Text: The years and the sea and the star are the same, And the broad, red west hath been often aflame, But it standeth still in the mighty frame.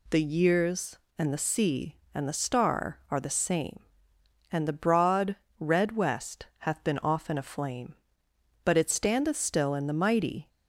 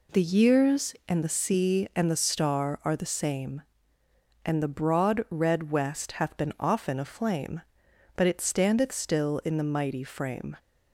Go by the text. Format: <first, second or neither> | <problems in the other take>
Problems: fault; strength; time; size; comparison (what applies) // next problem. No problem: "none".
second | stops before "frame"; at 10.4 s